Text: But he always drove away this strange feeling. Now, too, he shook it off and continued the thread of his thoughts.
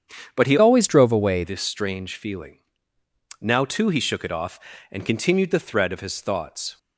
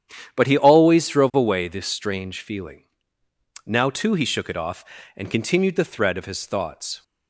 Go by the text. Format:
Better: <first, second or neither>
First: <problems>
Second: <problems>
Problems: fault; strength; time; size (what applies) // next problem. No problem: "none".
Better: second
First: starts louder than the rest; strong; until 1.3 s; 8 dB // changes voice from "always" to "away"; from 0.5 to 1.4 s; 0.9 s long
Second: starts louder than the rest; strong; until 1.4 s; 9.5 dB